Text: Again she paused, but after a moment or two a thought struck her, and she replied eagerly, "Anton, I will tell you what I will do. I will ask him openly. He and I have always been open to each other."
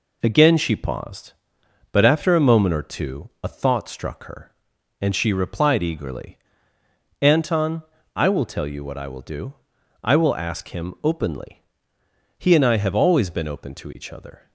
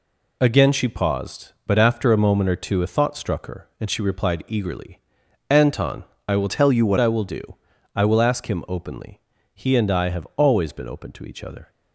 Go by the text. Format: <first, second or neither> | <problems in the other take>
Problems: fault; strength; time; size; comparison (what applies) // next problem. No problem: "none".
first | changes voice from "tell" to "what"; from 6.4 to 6.9 s; 0.5 s long